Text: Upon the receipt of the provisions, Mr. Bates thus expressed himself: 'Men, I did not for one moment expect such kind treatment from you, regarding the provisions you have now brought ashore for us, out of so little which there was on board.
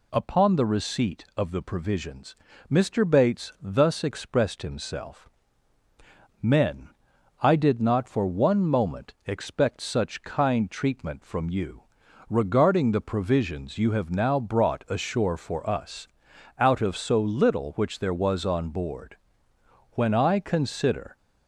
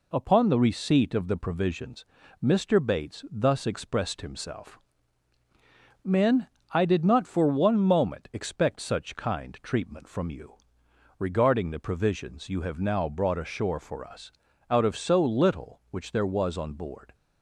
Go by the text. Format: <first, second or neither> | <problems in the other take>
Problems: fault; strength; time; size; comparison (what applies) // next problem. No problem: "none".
second | goes on to say "When I consider"; noticeable; from 19.9 s on; 1.2 s long